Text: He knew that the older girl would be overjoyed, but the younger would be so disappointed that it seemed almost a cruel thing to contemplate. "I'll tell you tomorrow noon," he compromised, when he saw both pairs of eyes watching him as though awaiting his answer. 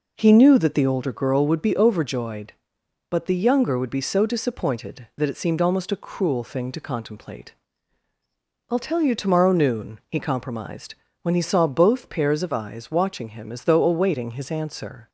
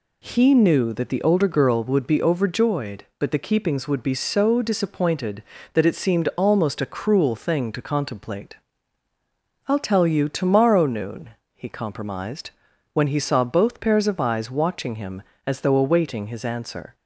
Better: first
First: none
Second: says "keepings" for "younger"; at 3.4 s

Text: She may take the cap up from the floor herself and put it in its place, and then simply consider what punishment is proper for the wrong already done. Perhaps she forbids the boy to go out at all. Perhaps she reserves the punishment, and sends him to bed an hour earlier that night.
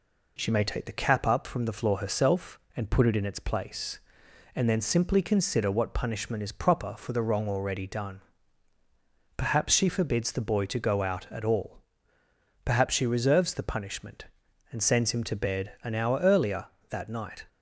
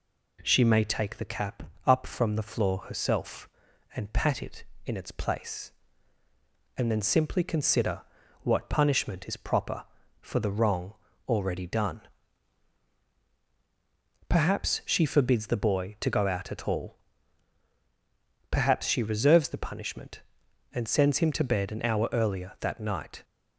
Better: first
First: none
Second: pauses between "cap" and "up"; slight; at 1.6 s; 0.22 s long // says "pat" for "put"; at 4.1 s // pauses between "consider" and "what"; at 8.0 s; 0.40 s long // pauses between "wrong" and "already"; slight; at 10.9 s; 0.34 s long

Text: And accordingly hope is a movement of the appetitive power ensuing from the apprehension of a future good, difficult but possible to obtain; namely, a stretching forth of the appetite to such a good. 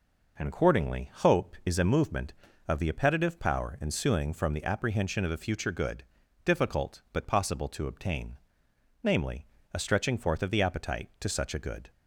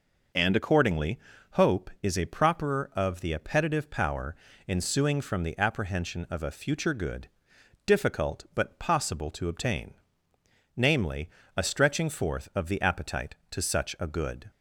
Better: first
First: none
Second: pauses between "accordingly" and "hope"; slight; at 1.1 s; 0.34 s long // says "properer" for "movement"; at 2.2 s // pauses between "power" and "ensuing"; slight; at 4.3 s; 0.32 s long

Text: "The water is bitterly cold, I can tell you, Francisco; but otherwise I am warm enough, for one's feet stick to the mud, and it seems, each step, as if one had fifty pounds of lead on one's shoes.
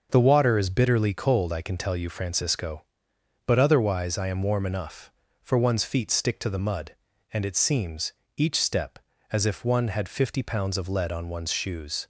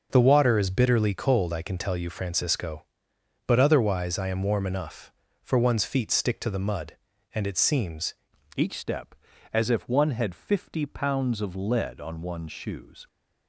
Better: first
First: starts louder than the rest; until 1.1 s; 6 dB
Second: starts louder than the rest; noticeable; until 1.1 s; 6 dB // changes voice at "each"; from 8.5 s on; 4.5 s long

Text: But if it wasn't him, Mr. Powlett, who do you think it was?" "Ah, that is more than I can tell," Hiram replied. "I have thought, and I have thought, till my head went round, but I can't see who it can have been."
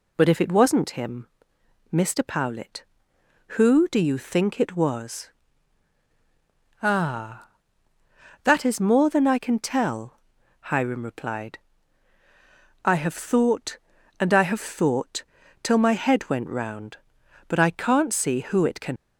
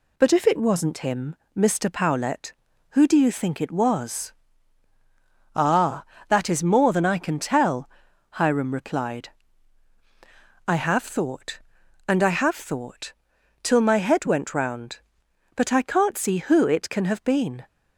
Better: second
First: stops before "have been"; at 18.9 s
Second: none

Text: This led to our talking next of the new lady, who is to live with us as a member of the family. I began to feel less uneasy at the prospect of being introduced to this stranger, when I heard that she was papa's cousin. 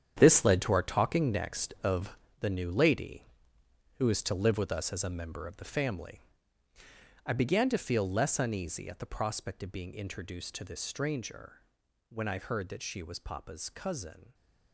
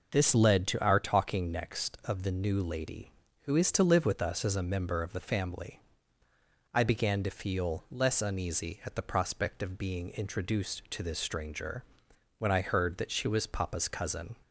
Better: second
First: gets quieter; strong; throughout; 12 dB // pauses between "of" and "the"; slight; at 2.1 s; 0.24 s long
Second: none

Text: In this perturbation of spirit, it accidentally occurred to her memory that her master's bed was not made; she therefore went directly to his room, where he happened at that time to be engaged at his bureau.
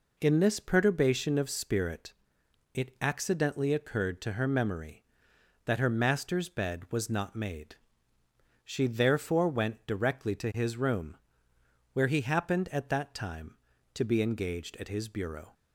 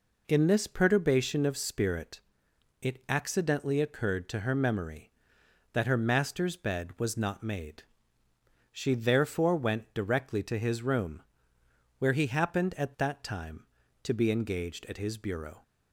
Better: neither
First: none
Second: none

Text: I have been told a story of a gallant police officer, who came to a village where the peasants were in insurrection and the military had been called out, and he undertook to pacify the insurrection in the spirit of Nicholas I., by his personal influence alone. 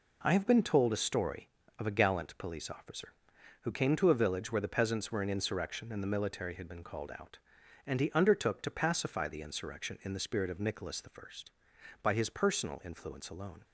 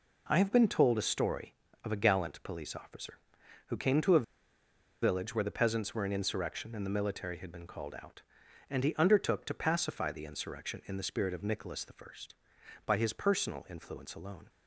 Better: first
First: none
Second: pauses between "a" and "village"; noticeable; at 4.2 s; 0.77 s long

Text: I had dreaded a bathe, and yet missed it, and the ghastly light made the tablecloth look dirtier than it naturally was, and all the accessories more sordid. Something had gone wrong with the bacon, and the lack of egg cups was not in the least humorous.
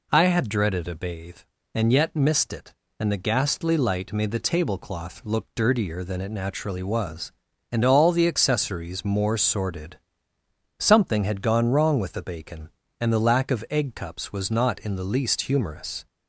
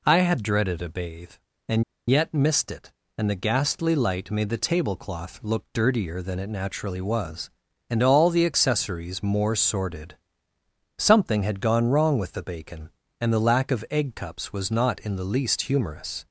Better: first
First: none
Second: pauses between "and" and "yet"; slight; at 1.8 s; 0.27 s long

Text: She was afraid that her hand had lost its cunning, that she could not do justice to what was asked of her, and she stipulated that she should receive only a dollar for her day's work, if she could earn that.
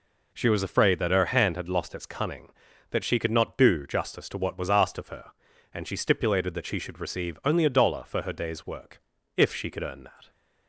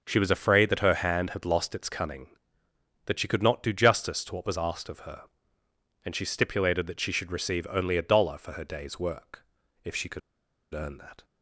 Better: first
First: none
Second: pauses between "could" and "earn"; noticeable; at 10.2 s; 0.53 s long

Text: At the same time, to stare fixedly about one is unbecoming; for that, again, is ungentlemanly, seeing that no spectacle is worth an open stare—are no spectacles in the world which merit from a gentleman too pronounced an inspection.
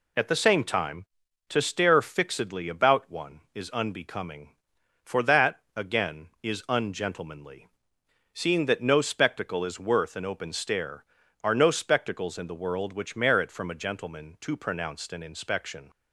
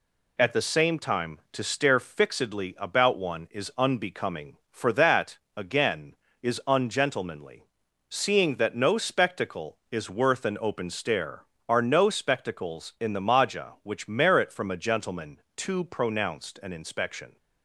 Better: first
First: none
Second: says "maja" for "world"; at 13.2 s

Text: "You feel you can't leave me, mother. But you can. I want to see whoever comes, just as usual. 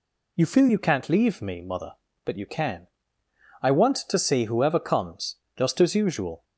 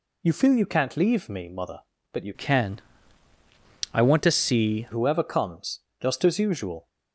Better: first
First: none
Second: changes voice from "can" to "see"; from 2.3 to 4.8 s; 2.5 s long

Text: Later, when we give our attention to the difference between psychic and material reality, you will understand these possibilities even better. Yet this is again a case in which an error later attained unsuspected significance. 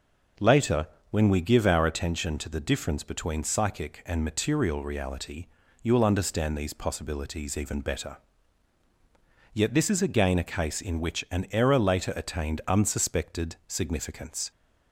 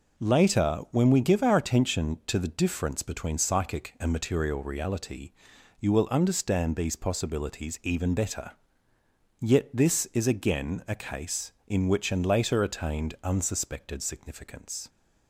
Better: first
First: none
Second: skips "error"; at 12.2 s

